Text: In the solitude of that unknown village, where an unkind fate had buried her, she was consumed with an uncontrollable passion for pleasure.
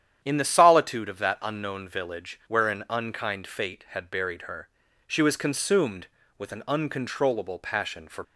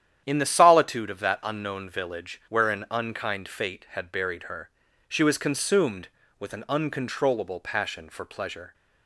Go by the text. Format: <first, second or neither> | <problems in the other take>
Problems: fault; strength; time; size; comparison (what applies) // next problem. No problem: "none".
second | starts louder than the rest; strong; until 1.2 s; 9.5 dB; strong in the second // stops before "pleasure"; at 8.2 s